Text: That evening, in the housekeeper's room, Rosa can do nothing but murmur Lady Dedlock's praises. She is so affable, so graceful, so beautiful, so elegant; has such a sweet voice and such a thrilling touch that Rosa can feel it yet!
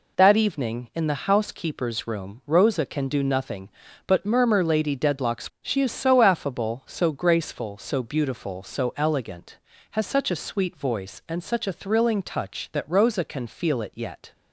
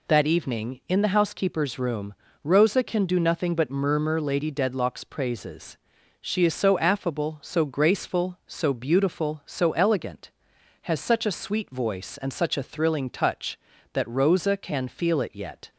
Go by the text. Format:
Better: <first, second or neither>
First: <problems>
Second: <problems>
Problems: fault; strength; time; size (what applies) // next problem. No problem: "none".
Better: second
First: skips "praises"; at 5.5 s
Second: none